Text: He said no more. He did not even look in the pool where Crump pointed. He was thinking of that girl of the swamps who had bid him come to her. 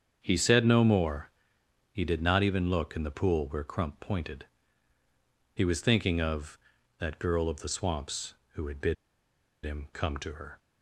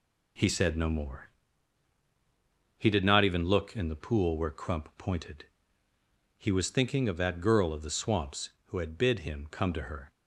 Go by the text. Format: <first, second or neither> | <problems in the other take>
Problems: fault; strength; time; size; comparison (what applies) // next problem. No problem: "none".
second | starts louder than the rest; strong; until 1.2 s; 7.5 dB // pauses between "bid" and "him"; noticeable; at 8.9 s; 0.68 s long